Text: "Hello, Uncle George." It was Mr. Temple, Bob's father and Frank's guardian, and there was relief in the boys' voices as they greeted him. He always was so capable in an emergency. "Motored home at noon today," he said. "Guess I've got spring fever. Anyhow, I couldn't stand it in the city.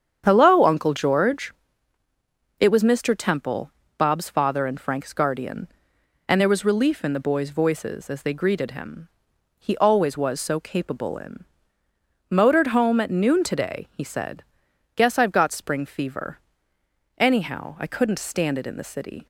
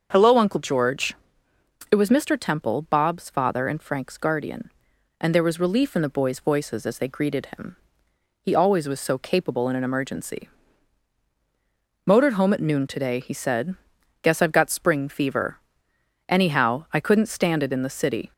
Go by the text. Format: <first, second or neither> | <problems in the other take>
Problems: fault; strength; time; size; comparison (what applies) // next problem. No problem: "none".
second | starts louder than the rest; strong; until 1.2 s; 8 dB; also in the second // skips "an emergency"; at 11.8 s